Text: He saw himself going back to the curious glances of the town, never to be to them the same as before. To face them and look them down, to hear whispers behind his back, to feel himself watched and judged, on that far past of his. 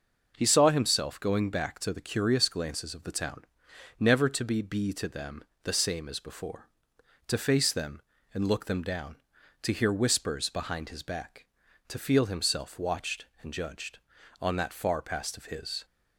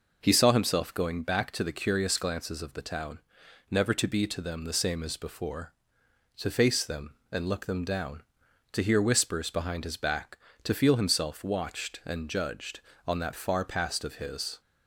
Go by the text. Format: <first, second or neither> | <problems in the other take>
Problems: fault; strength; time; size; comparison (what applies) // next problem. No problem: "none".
second | says "be" twice; at 4.6 s // pauses between "them" and "the"; slight; at 5.4 s; 0.20 s long